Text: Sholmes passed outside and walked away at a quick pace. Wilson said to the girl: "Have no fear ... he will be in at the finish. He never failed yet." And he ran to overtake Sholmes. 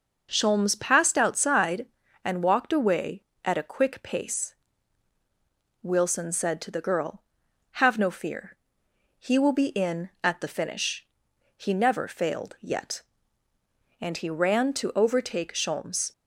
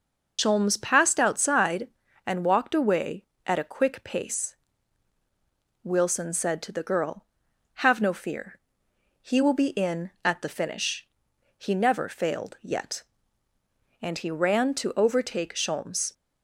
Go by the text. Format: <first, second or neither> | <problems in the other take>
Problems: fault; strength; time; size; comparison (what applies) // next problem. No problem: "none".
first | loses the start of "Sholmes"; at 0.3 s; 85 ms